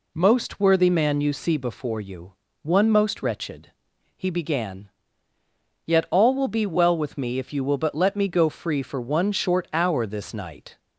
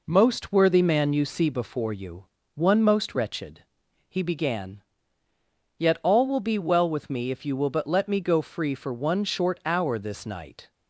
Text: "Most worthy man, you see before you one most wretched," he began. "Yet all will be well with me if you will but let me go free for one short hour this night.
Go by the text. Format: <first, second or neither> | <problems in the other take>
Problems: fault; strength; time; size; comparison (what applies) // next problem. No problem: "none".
first | gets quieter; throughout; 3.5 dB // pauses between "you" and "one"; slight; at 2.2 s; 0.30 s long; slight in the first